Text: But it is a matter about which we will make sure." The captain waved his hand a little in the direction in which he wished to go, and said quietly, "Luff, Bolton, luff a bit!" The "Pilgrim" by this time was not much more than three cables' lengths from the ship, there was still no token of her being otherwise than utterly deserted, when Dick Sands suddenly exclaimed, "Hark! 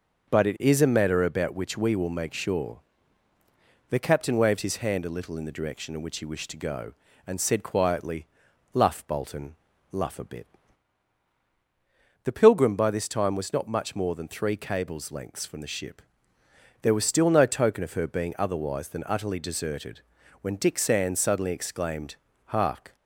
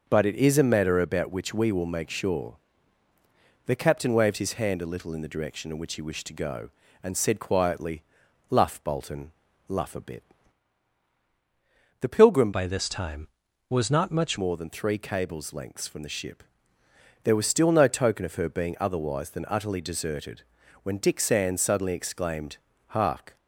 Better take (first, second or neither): first